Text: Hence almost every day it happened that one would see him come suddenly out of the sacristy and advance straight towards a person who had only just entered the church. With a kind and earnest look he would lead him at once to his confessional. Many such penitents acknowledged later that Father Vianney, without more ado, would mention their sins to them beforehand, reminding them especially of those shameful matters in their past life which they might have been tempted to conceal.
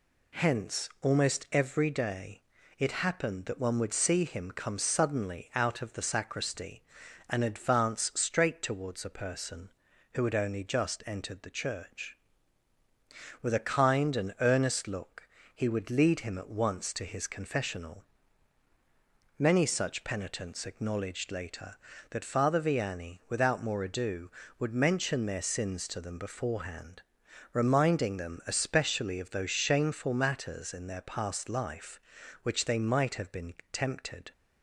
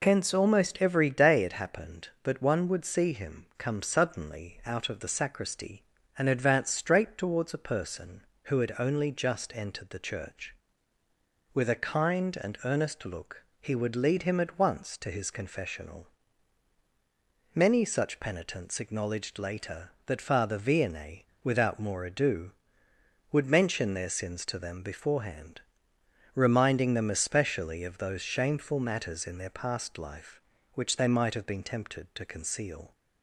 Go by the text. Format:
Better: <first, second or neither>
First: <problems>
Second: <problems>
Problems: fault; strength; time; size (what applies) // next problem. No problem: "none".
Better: second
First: pauses between "day" and "it"; at 2.4 s; 0.38 s long // pauses between "look" and "he"; slight; at 15.2 s; 0.26 s long // pauses between "been" and "tempted"; slight; at 33.5 s; 0.18 s long // stops before "to conceal"; at 34.3 s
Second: pauses between "look" and "he"; slight; at 13.4 s; 0.16 s long